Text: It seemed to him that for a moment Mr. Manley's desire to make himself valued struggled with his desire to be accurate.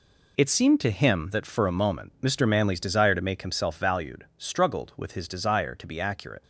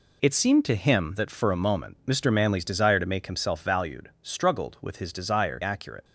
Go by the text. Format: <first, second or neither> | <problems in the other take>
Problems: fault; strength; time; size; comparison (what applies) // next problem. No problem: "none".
first | skips "to be"; at 5.6 s